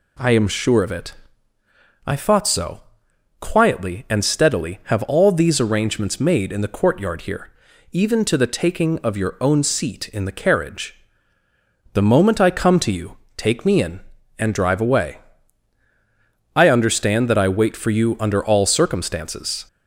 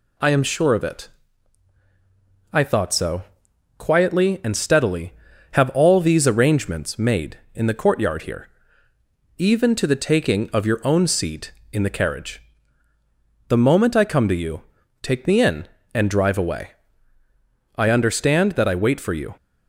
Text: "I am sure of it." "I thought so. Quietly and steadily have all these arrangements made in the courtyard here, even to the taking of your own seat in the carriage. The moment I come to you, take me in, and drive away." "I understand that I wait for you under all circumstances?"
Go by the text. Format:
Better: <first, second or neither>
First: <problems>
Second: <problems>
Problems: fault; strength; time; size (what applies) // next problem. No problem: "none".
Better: first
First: none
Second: stops before "under all circumstances"; at 19.3 s